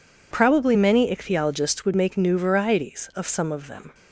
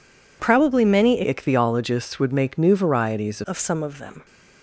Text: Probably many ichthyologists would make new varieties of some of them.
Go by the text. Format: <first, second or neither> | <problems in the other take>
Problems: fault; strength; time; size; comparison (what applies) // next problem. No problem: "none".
first | changes voice from "ichthyologists" to "varieties"; from 1.2 to 3.4 s; 2.2 s long